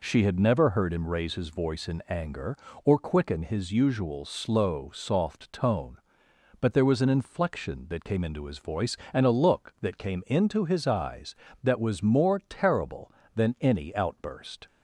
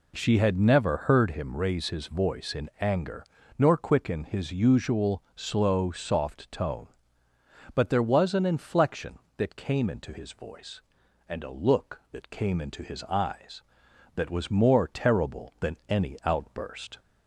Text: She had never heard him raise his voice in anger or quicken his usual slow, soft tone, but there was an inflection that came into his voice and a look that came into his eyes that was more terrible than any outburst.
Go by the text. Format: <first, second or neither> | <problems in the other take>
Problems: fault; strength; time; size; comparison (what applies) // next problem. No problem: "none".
first | says "nor" for "or"; at 3.5 s